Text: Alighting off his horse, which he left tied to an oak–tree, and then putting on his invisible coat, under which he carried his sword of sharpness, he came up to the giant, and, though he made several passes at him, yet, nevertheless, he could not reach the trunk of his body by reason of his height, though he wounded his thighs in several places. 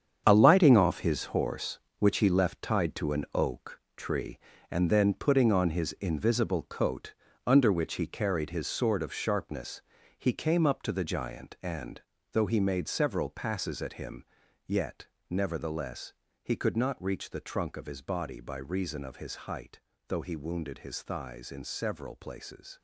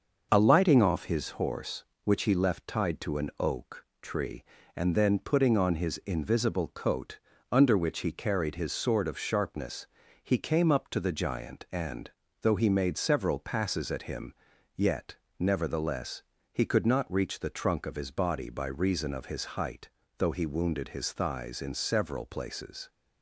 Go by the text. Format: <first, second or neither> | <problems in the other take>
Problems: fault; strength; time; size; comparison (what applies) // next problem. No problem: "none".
second | gets quieter; strong; throughout; 11 dB // starts louder than the rest; strong; until 1.2 s; 8 dB; also in the second